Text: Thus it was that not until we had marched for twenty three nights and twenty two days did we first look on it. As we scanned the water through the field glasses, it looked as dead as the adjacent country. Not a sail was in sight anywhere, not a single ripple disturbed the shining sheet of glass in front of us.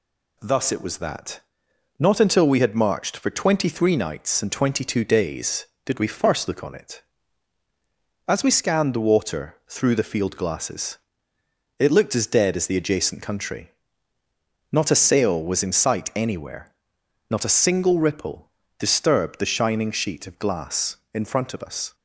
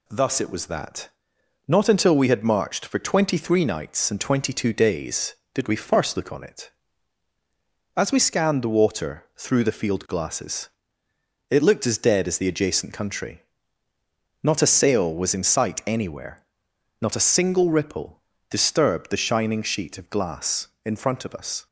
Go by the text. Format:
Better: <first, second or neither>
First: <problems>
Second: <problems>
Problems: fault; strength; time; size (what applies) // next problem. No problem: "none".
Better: neither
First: pauses between "that" and "not"; noticeable; at 1.3 s; 0.60 s long // pauses between "ripple" and "disturbed"; slight; at 18.4 s; 0.28 s long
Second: pauses between "that" and "not"; noticeable; at 1.0 s; 0.60 s long // pauses between "ripple" and "disturbed"; slight; at 18.2 s; 0.28 s long